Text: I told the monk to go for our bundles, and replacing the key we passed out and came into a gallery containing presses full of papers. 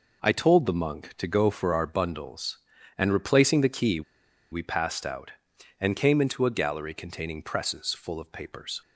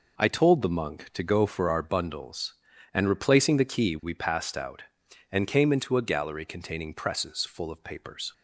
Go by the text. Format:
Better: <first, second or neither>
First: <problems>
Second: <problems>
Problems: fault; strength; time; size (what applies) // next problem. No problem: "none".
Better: second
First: pauses between "key" and "we"; noticeable; at 4.0 s; 0.49 s long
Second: none